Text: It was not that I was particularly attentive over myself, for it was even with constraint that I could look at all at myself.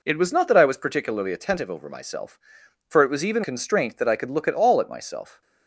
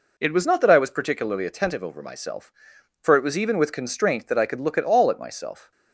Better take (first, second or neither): second